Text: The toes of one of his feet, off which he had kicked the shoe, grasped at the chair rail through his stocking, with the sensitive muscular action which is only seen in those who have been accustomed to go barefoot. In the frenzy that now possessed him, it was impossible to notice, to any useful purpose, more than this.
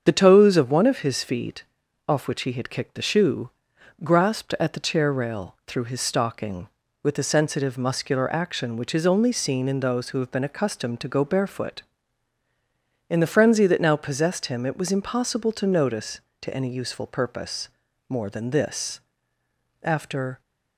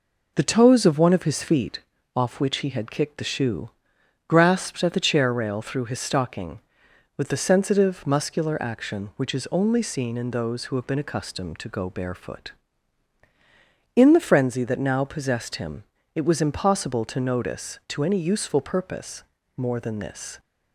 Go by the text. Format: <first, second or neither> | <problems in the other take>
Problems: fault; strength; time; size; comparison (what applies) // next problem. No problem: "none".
second | starts louder than the rest; strong; until 1.0 s; 7 dB // goes on to say "After"; from 19.8 s on; 0.58 s long